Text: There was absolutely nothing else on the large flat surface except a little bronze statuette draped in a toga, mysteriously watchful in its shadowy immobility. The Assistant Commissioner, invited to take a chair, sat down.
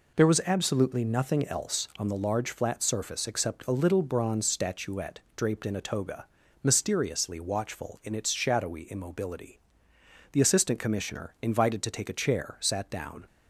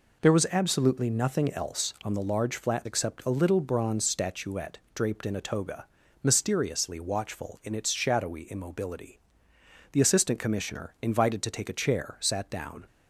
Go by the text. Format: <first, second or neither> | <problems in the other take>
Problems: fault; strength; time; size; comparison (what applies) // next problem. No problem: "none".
first | skips "surface"; at 2.8 s